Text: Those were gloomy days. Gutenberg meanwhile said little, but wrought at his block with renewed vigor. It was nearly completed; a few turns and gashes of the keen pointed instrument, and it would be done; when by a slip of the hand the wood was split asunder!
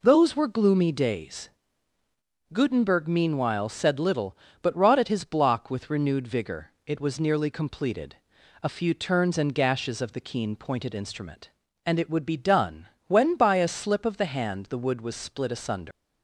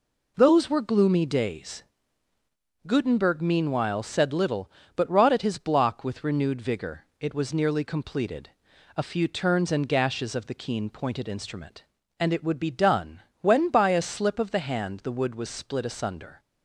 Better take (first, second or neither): second